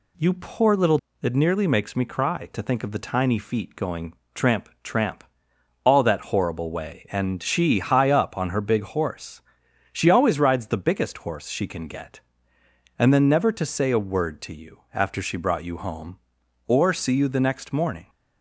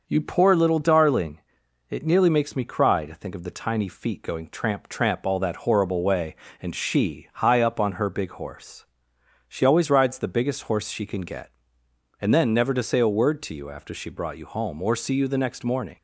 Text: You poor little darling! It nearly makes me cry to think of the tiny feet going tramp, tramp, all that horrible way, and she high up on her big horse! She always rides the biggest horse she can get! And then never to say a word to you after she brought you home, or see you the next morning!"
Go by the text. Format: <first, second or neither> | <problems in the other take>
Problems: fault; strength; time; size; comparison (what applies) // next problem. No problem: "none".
second | skips "darling"; at 1.0 s // pauses between "going" and "tramp"; slight; at 4.1 s; 0.20 s long